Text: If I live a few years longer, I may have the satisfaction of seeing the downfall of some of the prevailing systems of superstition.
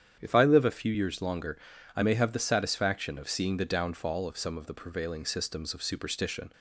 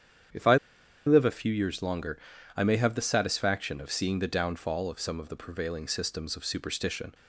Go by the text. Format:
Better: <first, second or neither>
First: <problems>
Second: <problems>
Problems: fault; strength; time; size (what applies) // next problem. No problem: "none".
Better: first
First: starts louder than the rest; strong; until 1.2 s; 9 dB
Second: starts louder than the rest; strong; until 1.8 s; 9 dB // pauses between "I" and "live"; noticeable; at 0.5 s; 0.50 s long